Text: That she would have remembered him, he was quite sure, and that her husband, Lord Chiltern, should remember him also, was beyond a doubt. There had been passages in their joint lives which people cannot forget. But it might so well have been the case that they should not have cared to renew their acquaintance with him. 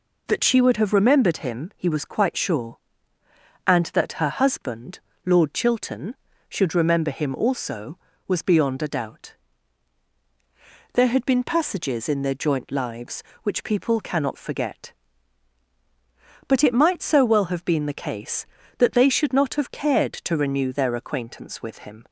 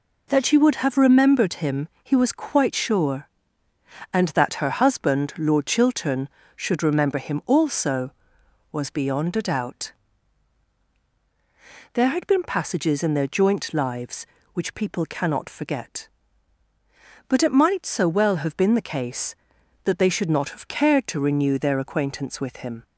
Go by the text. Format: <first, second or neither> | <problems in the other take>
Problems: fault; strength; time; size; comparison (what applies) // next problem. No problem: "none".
neither | none